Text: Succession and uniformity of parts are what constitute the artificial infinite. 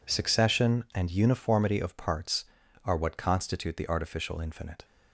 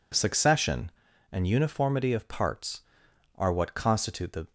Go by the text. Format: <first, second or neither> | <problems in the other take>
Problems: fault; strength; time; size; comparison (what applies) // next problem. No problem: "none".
first | stops before "artificial infinite"; at 4.4 s